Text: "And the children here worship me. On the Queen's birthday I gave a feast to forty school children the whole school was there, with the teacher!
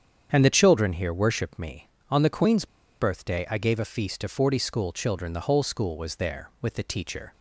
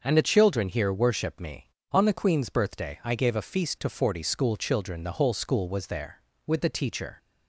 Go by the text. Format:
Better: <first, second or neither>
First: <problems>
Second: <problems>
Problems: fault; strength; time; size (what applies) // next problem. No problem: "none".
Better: second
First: starts louder than the rest; strong; until 1.3 s; 8 dB // pauses between "Queen's" and "birthday"; slight; at 2.6 s; 0.34 s long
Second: starts louder than the rest; until 1.0 s; 6.5 dB